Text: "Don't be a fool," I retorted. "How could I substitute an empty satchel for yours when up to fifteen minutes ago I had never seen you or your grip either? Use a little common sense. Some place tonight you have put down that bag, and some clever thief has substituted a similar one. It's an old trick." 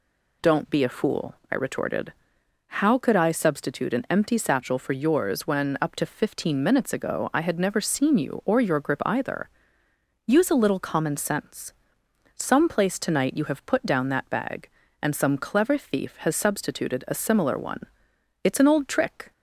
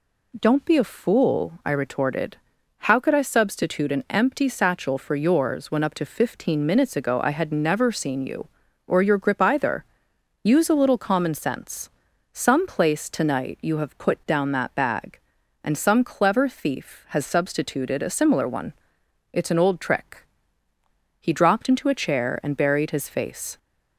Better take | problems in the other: first | goes on to say "He dropped into a chair and buried his face"; strong; from 21.1 s on; 2.3 s long

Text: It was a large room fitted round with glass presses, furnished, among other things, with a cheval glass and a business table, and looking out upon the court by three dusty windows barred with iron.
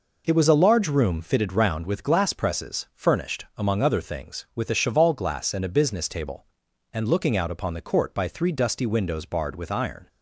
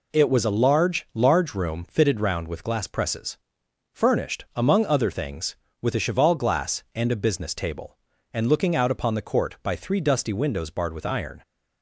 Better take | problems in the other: first | says "large" twice; at 1.1 s

